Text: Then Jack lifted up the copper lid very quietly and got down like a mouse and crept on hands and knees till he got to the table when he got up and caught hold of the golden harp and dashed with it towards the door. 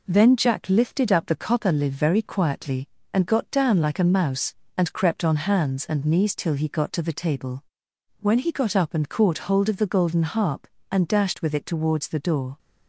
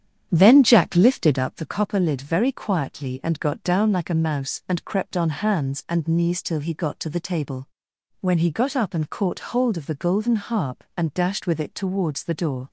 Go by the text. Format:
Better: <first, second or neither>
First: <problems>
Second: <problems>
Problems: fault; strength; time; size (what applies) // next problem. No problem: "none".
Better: first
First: pauses between "table" and "when"; noticeable; at 7.6 s; 0.56 s long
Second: starts louder than the rest; strong; until 1.7 s; 9 dB // pauses between "table" and "when"; noticeable; at 7.6 s; 0.52 s long